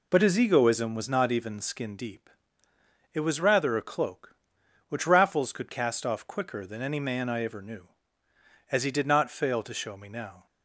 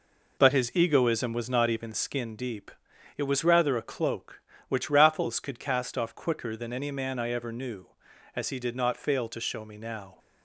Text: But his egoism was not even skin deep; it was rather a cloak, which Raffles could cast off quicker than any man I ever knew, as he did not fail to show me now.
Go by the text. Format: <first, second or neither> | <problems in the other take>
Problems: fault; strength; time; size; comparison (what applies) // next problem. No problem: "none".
neither | none